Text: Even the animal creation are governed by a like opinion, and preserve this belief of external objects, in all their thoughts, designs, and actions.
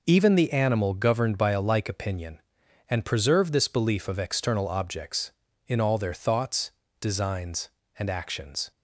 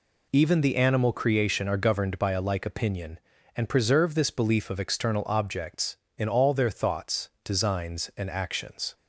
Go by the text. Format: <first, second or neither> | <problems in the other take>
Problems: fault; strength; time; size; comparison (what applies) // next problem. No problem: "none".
second | skips "creation are"; at 0.9 s